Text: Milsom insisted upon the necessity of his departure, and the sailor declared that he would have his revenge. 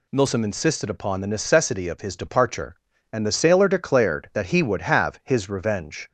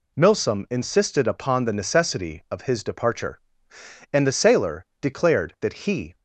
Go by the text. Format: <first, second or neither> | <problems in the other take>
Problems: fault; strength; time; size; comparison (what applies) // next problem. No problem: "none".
first | pauses between "sailor" and "declared"; slight; at 4.8 s; 0.16 s long // stops before "would have his revenge"; at 6.1 s